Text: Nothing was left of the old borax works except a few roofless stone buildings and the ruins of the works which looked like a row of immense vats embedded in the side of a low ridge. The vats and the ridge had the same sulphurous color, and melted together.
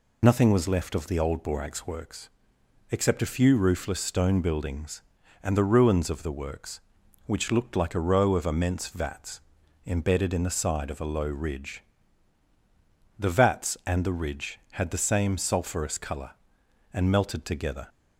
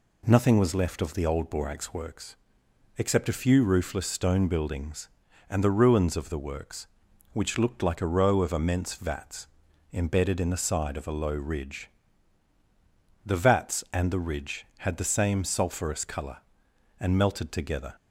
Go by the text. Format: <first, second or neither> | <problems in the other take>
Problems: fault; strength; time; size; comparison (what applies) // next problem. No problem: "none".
second | loses the start of "Nothing"; at 0.2 s; 65 ms // pauses between "works" and "except"; noticeable; at 2.2 s; 0.60 s long; noticeable in the second // pauses between "vats" and "embedded"; at 9.4 s; 0.44 s long; also in the second